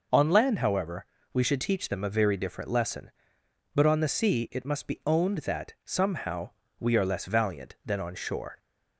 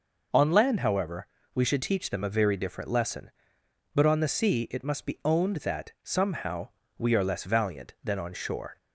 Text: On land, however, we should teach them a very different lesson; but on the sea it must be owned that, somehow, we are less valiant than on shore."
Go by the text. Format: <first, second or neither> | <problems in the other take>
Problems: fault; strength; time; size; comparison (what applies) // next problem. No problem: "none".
neither | none